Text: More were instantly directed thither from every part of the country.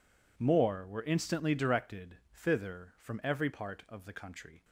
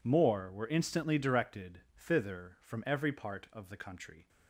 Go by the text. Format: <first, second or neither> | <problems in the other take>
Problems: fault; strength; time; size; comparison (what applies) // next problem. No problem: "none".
neither | pauses between "directed" and "thither"; slight; the same in both